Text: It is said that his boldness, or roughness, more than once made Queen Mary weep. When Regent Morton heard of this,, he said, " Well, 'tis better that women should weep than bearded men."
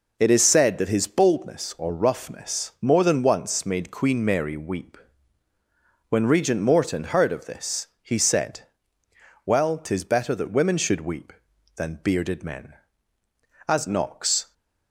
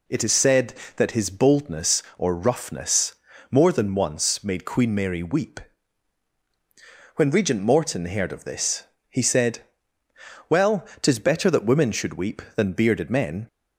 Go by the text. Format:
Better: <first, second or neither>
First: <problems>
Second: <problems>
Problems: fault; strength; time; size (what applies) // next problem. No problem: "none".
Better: second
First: goes on to say "As Knox"; noticeable; from 13.6 s on; 0.85 s long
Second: none